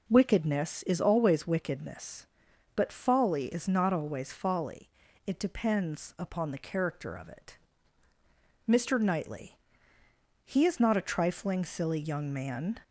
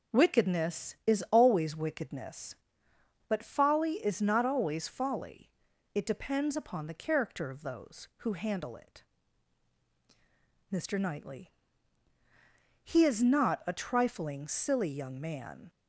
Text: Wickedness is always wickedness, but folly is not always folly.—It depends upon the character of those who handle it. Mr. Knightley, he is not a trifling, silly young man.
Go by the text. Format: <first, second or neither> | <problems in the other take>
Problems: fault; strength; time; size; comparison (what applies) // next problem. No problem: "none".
second | skips "those who handle"; at 7.2 s